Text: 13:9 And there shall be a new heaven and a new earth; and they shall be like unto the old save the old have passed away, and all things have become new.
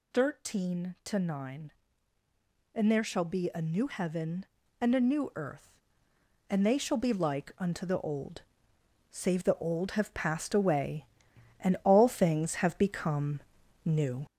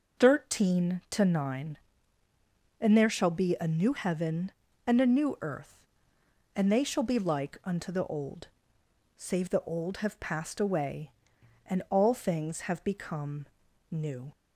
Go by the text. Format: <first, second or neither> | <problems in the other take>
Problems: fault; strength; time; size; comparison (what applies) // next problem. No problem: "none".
second | gets louder; noticeable; throughout; 4.5 dB // pauses between "old" and "save"; noticeable; at 8.4 s; 0.68 s long; noticeable in the second // pauses between "become" and "new"; noticeable; at 13.3 s; 0.46 s long; noticeable in the second